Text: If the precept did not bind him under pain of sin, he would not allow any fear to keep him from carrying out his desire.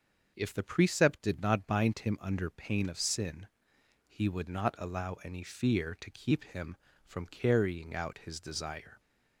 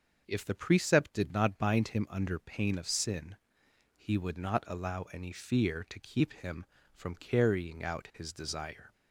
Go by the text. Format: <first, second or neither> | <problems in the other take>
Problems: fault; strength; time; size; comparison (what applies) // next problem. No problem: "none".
neither | starts louder than the rest; the same in both